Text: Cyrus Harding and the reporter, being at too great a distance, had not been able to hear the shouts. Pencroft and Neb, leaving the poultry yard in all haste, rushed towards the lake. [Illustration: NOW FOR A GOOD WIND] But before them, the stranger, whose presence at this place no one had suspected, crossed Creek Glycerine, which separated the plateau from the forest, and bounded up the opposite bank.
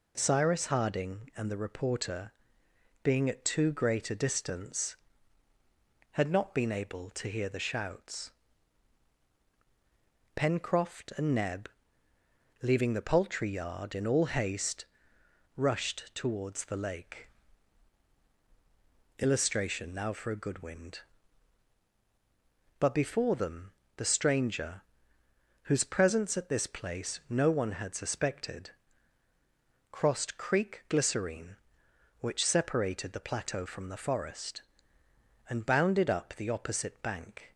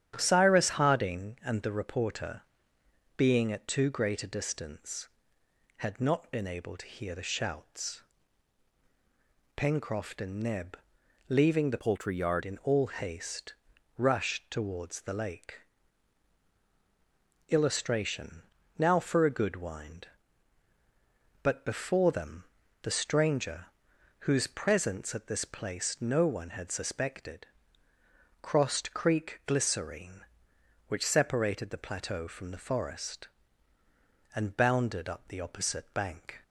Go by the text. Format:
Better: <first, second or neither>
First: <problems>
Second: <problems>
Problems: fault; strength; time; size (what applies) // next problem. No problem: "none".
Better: first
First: none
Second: starts louder than the rest; strong; until 1.1 s; 10 dB // changes voice from "poultry" to "yard"; from 11.7 to 12.4 s; 0.7 s long